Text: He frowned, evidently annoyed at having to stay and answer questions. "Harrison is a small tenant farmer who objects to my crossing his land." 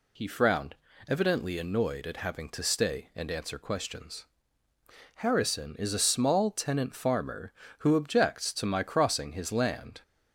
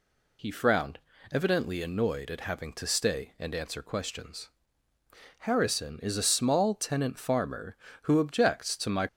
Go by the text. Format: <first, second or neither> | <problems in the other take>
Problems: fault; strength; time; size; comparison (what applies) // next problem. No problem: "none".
first | stops before "crossing his land"; at 9.0 s